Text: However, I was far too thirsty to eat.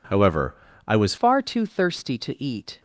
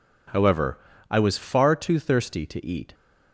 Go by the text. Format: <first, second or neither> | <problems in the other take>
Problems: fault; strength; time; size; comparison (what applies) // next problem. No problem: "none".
second | changes voice at "far"; from 1.1 s on; 1.7 s long